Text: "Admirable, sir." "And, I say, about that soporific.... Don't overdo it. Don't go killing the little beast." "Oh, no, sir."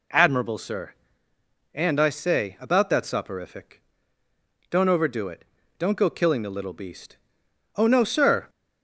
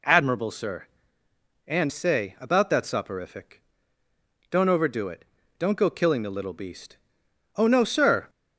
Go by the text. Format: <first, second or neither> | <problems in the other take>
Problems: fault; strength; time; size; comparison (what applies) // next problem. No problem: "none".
first | skips "I"; at 1.8 s